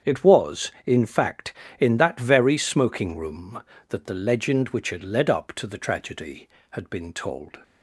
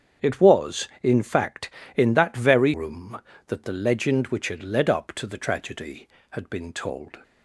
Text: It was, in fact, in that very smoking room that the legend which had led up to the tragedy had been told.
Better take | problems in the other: first | starts louder than the rest; strong; until 1.3 s; 7 dB; strong in the first // skips "smoking"; at 2.7 s

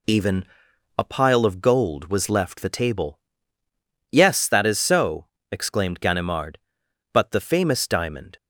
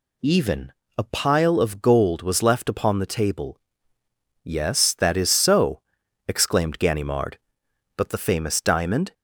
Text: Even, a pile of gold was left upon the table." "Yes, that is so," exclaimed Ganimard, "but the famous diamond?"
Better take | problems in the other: second | skips "upon"; at 2.5 s

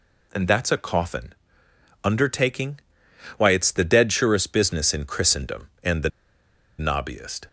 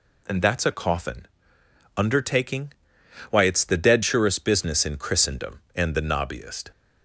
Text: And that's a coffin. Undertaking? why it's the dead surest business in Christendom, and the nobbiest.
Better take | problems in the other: second | pauses between "the" and "nobbiest"; noticeable; at 6.0 s; 0.70 s long

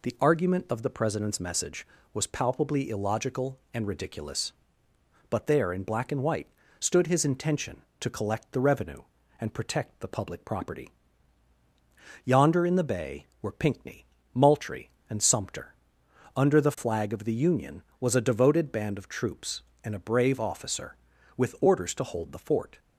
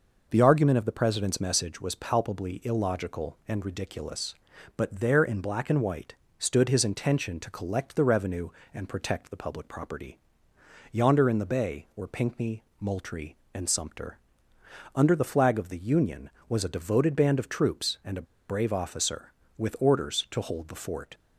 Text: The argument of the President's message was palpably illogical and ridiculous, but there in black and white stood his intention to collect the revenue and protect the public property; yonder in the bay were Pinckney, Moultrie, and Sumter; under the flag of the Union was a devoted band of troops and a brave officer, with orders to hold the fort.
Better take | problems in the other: first | pauses between "white" and "stood"; slight; at 6.1 s; 0.22 s long; slight in the first // pauses between "a" and "brave"; slight; at 18.2 s; 0.23 s long

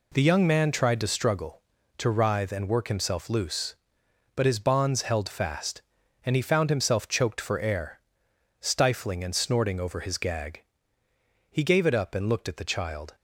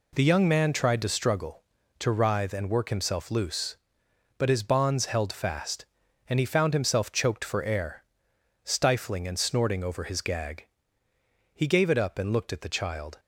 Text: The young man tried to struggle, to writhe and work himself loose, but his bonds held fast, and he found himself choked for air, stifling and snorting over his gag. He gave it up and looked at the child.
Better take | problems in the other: neither | none

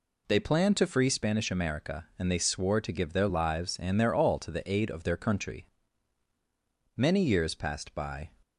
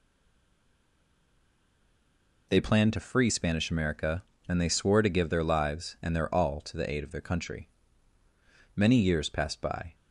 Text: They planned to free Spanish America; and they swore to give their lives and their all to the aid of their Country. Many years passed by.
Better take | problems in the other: first | stays silent before the first word; until 2.4 s; 2.4 s long

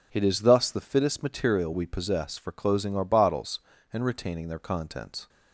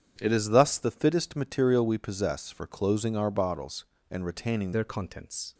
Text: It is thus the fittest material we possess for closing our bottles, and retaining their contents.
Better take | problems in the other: first | starts louder than the rest; strong; until 1.1 s; 8.5 dB // changes voice at "their"; from 4.7 s on; 0.8 s long

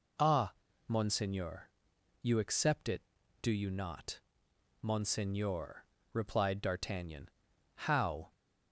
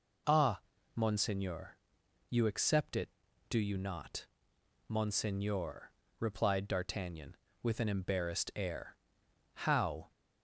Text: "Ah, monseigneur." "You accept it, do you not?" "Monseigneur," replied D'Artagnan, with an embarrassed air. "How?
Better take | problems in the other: second | skips "with an embarrassed air"; at 7.5 s

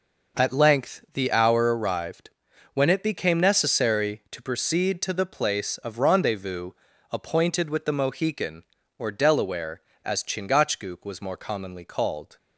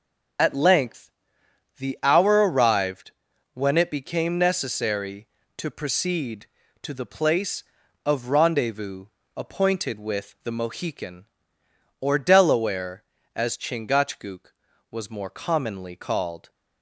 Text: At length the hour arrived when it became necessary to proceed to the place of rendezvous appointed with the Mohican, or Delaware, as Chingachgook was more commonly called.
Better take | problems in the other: first | loses the start of "At"; at 0.3 s; 55 ms // pauses between "length" and "the"; noticeable; at 1.1 s; 0.66 s long // pauses between "arrived" and "when"; at 3.1 s; 0.42 s long; also in the first // pauses between "rendezvous" and "appointed"; slight; at 9.0 s; 0.30 s long; also in the first

